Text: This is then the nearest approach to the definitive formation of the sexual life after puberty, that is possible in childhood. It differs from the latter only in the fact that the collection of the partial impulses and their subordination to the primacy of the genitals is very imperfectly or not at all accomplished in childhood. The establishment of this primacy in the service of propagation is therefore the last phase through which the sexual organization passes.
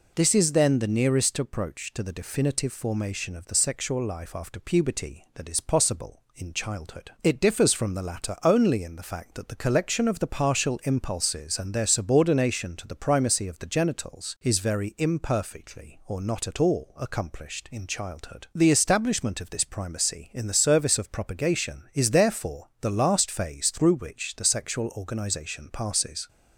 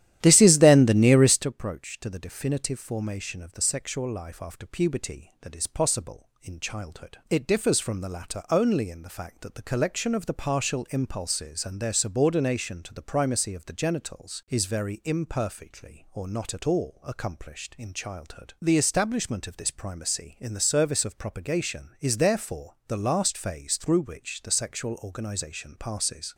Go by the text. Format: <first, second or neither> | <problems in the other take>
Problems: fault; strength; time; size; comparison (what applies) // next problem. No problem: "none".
first | starts louder than the rest; strong; until 1.5 s; 12 dB